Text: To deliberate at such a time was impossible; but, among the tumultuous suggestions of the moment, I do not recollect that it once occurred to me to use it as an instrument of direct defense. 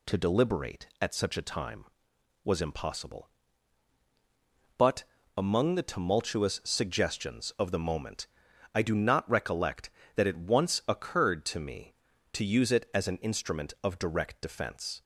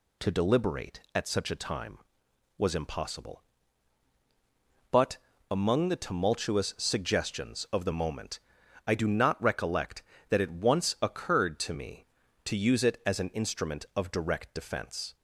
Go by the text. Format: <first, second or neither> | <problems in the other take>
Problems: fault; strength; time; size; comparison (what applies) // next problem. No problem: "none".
neither | none